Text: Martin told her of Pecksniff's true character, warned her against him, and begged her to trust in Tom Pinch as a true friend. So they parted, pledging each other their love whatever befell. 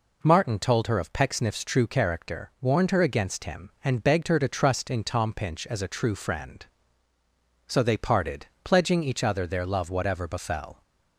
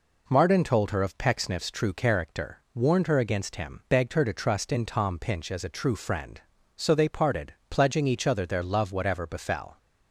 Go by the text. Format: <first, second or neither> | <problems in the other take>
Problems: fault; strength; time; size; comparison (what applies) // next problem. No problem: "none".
first | skips "and"; at 3.8 s